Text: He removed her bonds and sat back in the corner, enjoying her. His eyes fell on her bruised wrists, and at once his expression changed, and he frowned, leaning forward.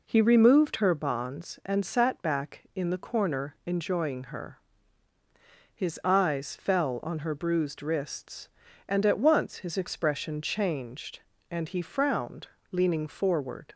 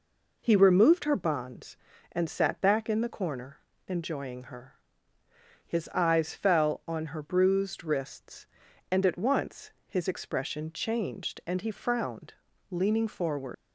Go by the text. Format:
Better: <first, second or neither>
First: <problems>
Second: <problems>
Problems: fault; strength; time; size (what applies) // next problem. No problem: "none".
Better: first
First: none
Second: pauses between "once" and "his"; slight; at 9.7 s; 0.16 s long // leaves "forward" unfinished; at 13.5 s; 100 ms